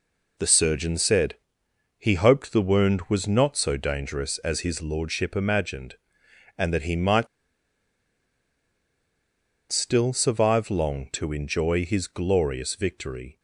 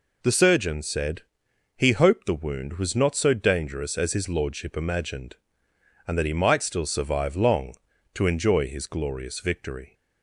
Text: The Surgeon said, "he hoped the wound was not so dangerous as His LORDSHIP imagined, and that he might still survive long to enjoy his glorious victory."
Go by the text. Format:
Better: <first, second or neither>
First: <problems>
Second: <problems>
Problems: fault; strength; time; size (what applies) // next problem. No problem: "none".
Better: second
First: pauses between "might" and "still"; strong; at 7.2 s; 2.4 s long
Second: none